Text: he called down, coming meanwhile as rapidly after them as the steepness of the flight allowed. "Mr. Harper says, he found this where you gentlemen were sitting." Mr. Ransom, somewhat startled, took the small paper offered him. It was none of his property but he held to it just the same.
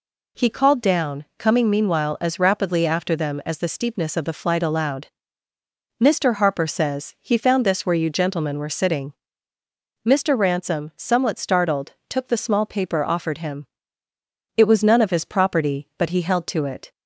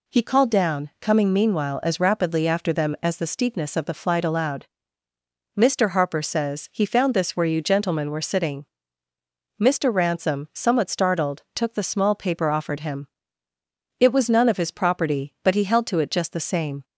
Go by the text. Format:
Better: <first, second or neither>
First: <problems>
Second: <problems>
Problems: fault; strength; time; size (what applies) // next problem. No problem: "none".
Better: second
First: stops before "just the same"; at 16.9 s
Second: none